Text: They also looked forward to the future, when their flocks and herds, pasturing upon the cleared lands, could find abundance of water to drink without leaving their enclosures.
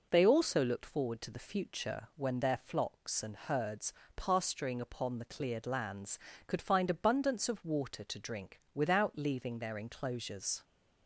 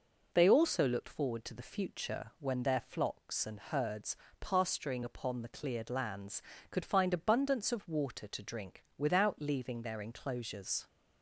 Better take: neither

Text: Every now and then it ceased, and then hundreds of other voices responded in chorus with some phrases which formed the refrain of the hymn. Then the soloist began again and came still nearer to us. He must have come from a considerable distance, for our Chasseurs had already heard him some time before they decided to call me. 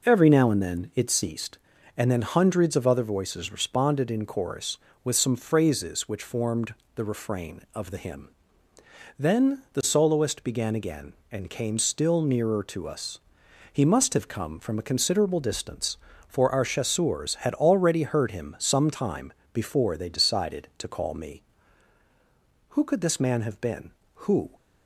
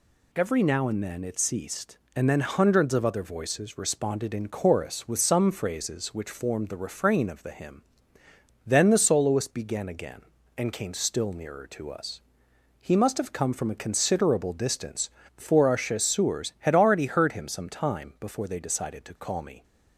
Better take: second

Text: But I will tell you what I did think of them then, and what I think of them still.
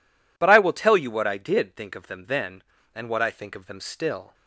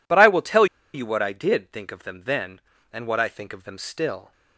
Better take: first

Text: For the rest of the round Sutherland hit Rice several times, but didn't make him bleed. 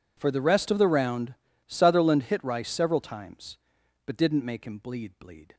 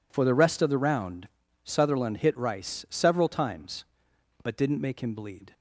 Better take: second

